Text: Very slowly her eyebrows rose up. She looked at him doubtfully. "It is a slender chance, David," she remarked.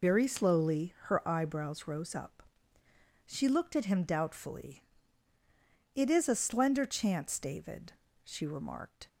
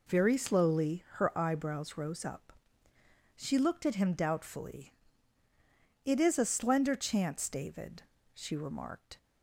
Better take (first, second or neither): second